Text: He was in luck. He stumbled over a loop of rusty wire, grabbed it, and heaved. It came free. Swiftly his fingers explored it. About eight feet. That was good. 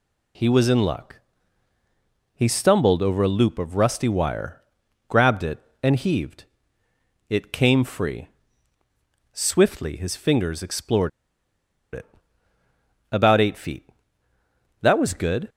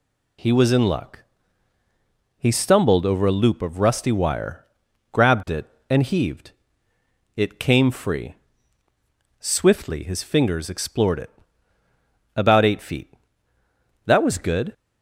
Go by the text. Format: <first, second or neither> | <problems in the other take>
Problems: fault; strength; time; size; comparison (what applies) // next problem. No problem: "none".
second | pauses between "explored" and "it"; noticeable; at 11.0 s; 0.82 s long